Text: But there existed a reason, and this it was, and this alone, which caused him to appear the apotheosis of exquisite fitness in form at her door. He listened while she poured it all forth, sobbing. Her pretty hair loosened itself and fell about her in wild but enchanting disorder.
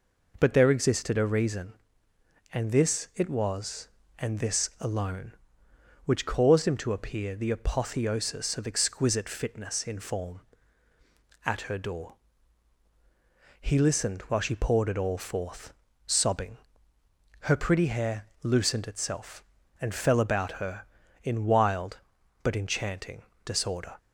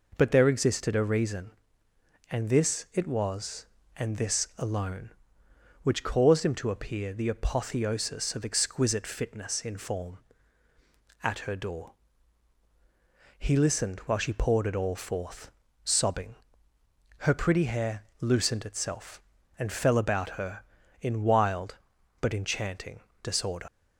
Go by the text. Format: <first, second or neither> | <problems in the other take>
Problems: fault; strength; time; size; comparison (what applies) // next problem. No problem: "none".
first | pauses between "hair" and "loosened"; slight; at 18.0 s; 0.18 s long; slight in the first // pauses between "enchanting" and "disorder"; slight; at 22.9 s; 0.24 s long; slight in the first // leaves "disorder" unfinished; at 23.6 s; 70 ms